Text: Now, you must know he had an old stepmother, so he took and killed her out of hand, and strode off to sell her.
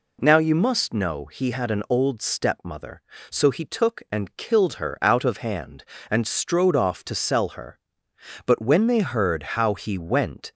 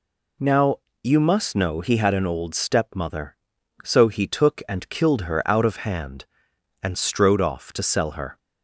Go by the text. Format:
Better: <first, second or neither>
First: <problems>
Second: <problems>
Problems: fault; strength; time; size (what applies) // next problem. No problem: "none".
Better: second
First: goes on to say "But when they heard how he went"; strong; from 8.4 s on; 2.0 s long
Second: none